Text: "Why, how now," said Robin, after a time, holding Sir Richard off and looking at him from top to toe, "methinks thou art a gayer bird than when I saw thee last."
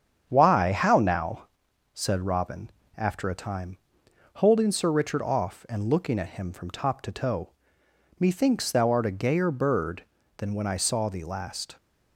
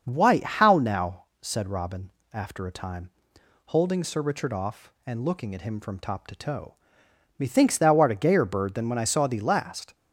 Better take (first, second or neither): second